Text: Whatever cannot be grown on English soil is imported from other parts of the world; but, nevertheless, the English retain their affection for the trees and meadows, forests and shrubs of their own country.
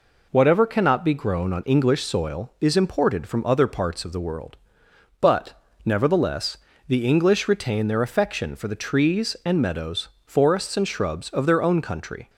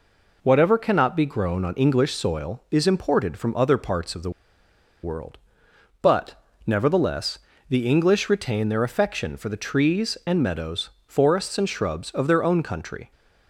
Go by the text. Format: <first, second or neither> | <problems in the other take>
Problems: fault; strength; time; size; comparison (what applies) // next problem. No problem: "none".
first | pauses between "the" and "world"; noticeable; at 4.2 s; 0.73 s long